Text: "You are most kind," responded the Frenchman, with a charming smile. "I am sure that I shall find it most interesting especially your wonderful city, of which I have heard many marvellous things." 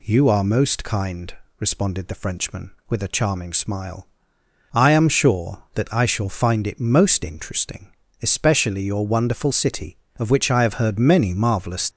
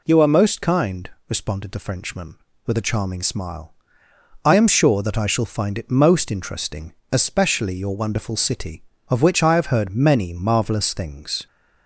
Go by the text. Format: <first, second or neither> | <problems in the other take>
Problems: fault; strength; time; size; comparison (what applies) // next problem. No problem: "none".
second | pauses between "interesting" and "especially"; slight; at 7.9 s; 0.32 s long; slight in the second // stops before "things"; at 11.9 s